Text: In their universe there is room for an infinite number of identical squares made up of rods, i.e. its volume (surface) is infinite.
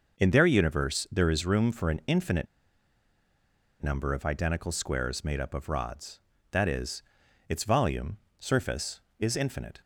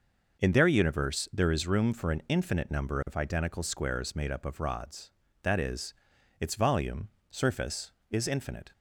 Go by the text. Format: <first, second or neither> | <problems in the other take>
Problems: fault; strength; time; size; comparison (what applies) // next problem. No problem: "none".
second | pauses between "infinite" and "number"; strong; at 2.4 s; 1.3 s long